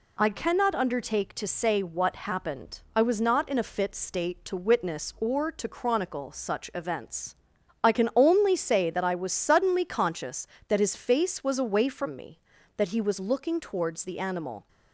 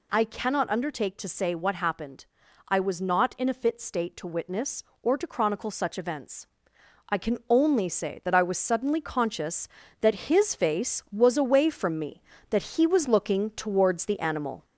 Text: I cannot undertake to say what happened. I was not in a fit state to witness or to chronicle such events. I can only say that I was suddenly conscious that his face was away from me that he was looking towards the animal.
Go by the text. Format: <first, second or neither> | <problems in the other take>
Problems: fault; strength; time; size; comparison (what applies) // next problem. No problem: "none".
first | gets louder; throughout; 3.5 dB